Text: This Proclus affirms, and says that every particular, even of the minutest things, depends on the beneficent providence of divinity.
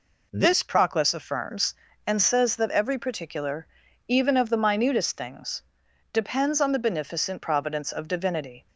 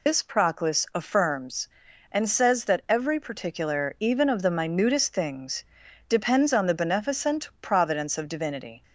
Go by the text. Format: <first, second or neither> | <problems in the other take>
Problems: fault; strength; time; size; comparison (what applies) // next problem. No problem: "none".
first | loses the start of "This"; at 0.0 s; 115 ms